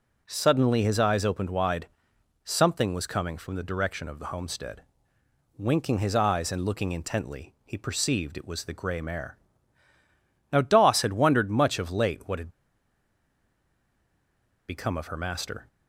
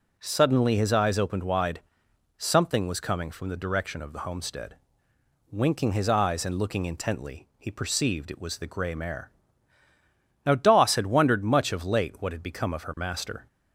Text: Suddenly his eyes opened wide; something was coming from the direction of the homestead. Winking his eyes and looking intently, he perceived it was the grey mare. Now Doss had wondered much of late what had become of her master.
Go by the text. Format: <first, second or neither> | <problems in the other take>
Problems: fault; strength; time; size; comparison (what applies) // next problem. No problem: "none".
second | pauses between "had" and "become"; strong; at 12.4 s; 2.1 s long